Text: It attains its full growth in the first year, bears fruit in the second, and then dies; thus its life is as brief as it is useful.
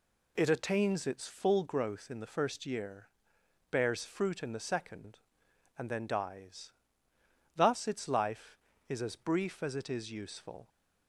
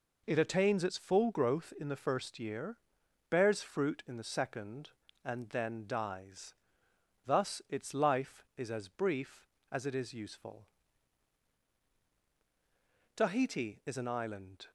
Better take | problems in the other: first | goes on to say "Tahiti is an island"; from 13.1 s on; 1.5 s long

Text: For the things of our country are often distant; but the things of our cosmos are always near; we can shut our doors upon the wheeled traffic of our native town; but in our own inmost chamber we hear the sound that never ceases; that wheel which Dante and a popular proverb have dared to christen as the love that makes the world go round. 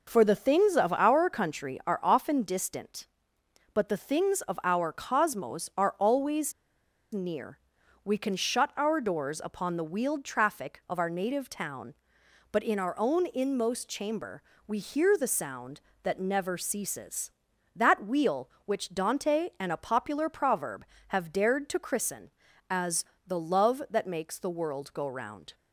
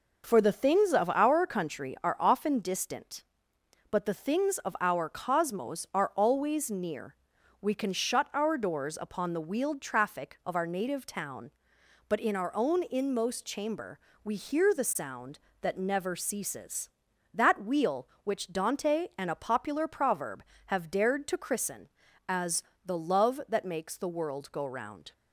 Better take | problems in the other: second | pauses between "always" and "near"; noticeable; at 6.5 s; 0.61 s long // pauses between "chamber" and "we"; slight; at 14.4 s; 0.24 s long; slight in the second // pauses between "as" and "the"; slight; at 23.0 s; 0.20 s long; slight in the second

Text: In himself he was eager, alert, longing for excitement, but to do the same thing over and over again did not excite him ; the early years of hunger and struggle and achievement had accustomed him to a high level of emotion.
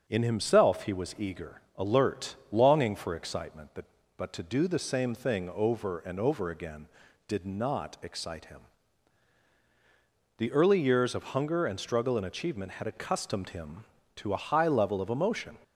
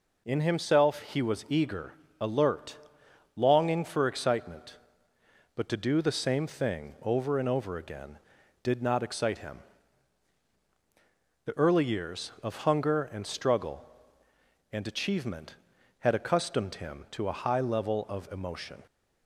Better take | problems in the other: second | starts louder than the rest; until 1.0 s; 6.5 dB // says "but" twice; at 4.1 s

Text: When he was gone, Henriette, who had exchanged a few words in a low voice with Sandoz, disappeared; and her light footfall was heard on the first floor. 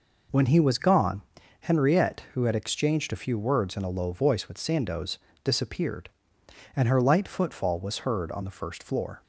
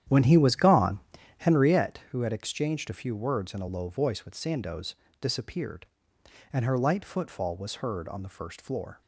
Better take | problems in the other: first | starts louder than the rest; strong; until 1.9 s; 10 dB

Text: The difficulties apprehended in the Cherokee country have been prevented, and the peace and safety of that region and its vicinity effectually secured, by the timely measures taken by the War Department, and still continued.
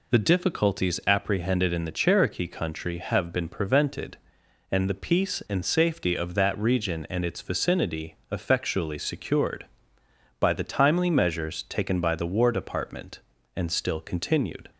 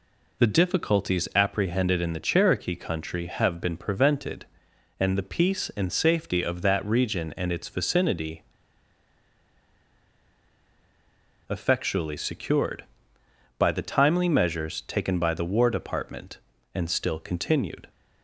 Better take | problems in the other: first | pauses between "vicinity" and "effectually"; strong; at 8.4 s; 3.0 s long

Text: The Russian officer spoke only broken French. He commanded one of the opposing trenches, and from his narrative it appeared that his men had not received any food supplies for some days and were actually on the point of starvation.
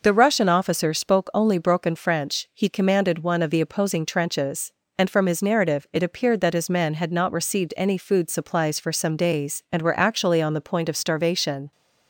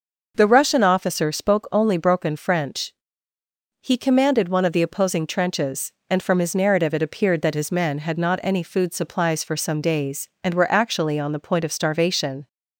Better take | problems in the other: first | skips "received"; at 8.4 s

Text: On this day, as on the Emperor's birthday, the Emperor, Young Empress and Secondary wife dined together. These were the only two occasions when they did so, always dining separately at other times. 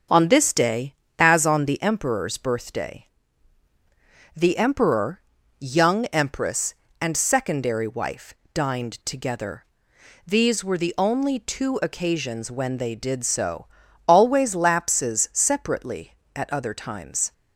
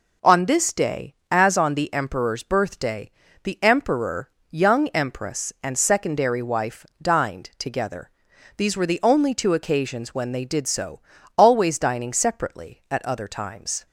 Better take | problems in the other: second | starts louder than the rest; until 1.3 s; 6.5 dB // pauses between "wife" and "dined"; slight; at 8.3 s; 0.22 s long; slight in the second // says "lapses" for "dining"; at 14.5 s

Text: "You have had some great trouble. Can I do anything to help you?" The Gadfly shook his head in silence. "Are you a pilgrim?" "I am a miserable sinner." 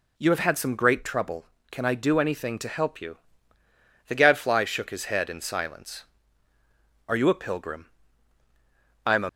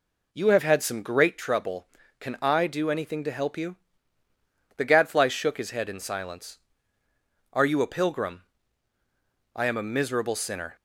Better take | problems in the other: second | stops before "miserable sinner"; at 9.2 s

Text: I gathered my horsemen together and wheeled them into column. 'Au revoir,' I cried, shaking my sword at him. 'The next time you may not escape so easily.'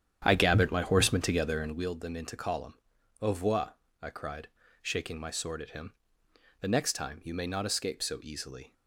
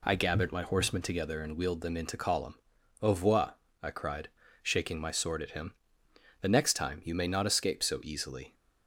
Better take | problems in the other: second | starts louder than the rest; strong; until 1.9 s; 9.5 dB

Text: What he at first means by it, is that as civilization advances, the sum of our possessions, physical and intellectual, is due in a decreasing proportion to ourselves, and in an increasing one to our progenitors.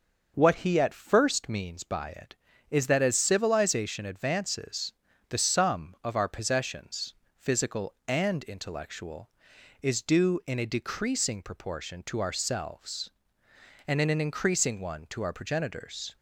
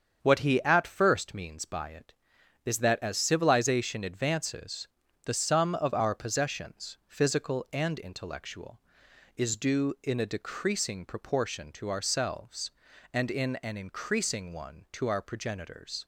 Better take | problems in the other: neither | starts louder than the rest; the same in both

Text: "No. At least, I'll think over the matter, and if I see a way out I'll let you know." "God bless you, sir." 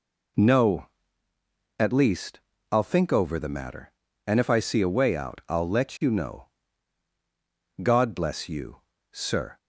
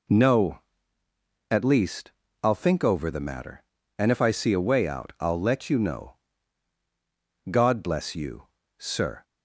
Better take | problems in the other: neither | none

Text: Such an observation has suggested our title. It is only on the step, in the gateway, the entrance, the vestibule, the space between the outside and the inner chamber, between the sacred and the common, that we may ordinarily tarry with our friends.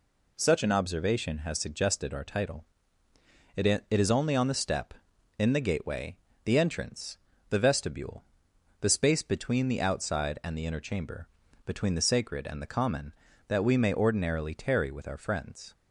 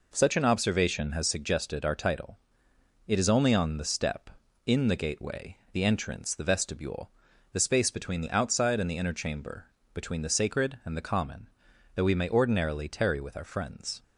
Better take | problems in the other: second | says "It" twice; at 3.6 s

